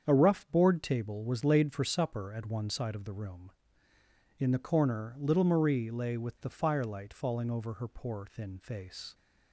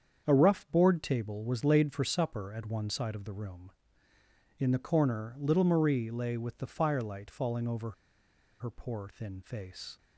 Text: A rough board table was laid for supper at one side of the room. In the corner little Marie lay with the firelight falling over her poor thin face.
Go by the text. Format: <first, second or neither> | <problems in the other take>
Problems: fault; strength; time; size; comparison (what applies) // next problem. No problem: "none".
first | starts louder than the rest; strong; until 1.2 s; 7.5 dB; strong in the first // pauses between "over" and "her"; noticeable; at 7.9 s; 0.68 s long